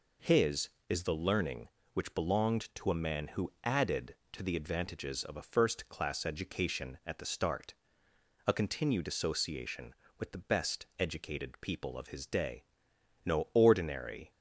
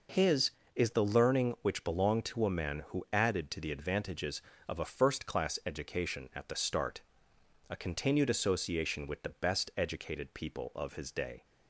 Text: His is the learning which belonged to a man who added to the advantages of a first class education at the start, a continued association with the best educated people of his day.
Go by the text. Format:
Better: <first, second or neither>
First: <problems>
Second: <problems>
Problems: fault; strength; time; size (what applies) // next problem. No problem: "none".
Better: second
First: goes on to say "No ordinary"; noticeable; from 13.2 s on; 1.0 s long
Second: none